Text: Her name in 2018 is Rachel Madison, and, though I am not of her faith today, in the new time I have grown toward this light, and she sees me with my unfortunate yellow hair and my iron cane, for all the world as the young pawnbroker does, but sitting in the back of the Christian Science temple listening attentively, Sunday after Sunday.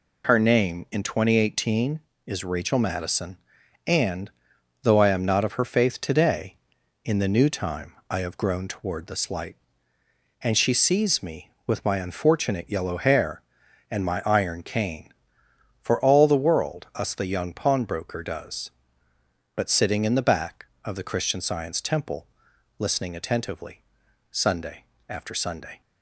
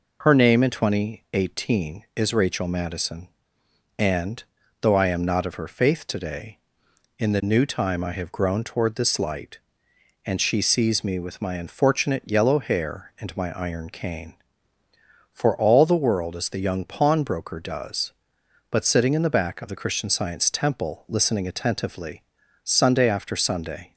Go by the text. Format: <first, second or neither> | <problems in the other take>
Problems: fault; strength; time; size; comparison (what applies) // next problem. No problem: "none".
second | pauses between "time" and "I"; slight; at 7.9 s; 0.16 s long // says "us" for "as"; at 16.9 s // pauses between "temple" and "listening"; noticeable; at 22.2 s; 0.52 s long // pauses between "Sunday" and "after"; slight; at 24.8 s; 0.22 s long